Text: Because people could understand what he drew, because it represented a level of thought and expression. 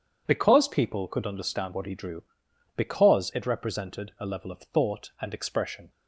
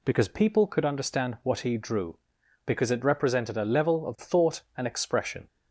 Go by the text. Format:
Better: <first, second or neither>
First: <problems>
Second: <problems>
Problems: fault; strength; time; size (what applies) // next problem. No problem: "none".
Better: neither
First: none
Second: none